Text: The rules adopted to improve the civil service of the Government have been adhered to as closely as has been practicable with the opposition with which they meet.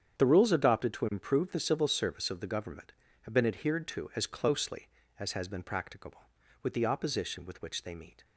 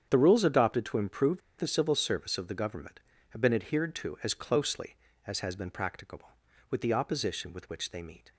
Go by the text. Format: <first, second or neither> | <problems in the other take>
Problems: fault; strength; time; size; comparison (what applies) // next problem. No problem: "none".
first | starts louder than the rest; strong; until 1.1 s; 8.5 dB; strong in the first // pauses between "improve" and "the"; slight; at 1.4 s; 0.19 s long